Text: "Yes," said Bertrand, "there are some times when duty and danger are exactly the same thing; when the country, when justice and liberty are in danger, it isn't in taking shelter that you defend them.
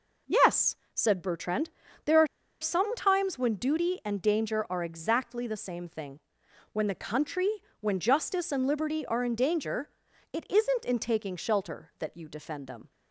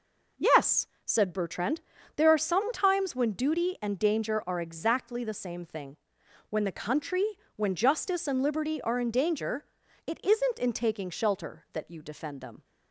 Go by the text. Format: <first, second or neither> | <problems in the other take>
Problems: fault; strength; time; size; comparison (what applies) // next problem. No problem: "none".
second | pauses between "are" and "some"; slight; at 2.2 s; 0.35 s long